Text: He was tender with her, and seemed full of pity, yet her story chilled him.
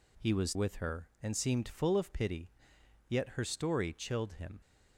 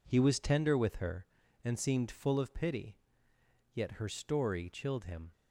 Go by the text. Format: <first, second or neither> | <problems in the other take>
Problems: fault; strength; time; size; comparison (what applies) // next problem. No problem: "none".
second | skips "tender"; at 0.5 s